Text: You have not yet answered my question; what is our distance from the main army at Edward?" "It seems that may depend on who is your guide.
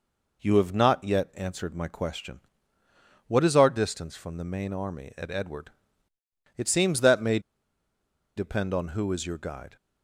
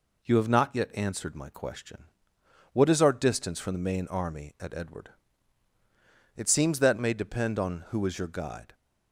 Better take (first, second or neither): second